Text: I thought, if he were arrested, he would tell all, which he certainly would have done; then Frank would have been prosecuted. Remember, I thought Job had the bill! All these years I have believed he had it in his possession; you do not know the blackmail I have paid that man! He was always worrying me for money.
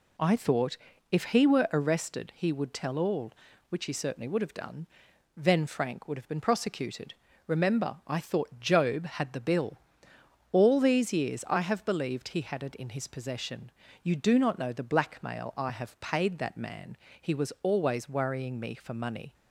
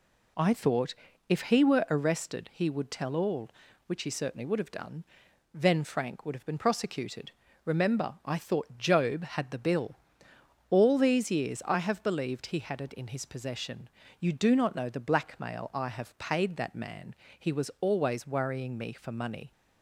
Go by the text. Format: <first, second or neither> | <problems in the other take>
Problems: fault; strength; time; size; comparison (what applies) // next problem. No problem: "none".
neither | none